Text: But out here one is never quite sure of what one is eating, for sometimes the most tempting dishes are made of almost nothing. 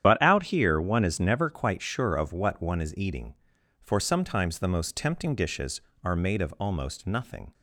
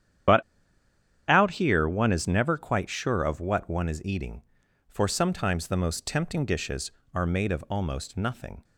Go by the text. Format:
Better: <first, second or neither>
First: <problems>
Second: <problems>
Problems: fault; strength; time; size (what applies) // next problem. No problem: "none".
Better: first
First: starts louder than the rest; strong; until 1.0 s; 9.5 dB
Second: starts louder than the rest; strong; until 2.1 s; 9.5 dB // pauses between "But" and "out"; noticeable; at 0.4 s; 0.86 s long